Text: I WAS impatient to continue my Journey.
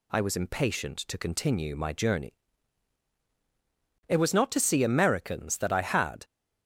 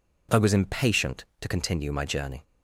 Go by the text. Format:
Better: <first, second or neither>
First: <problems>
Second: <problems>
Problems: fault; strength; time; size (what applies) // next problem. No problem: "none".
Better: second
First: goes on to say "It was not to see Americans that I had"; strong; from 4.0 s on; 2.1 s long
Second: none